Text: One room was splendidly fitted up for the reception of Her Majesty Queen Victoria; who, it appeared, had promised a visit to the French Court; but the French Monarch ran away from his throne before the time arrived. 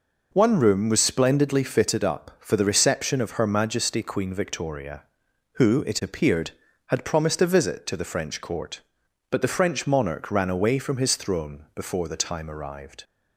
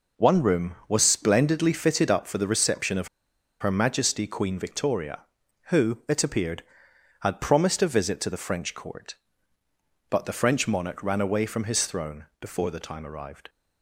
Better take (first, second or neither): first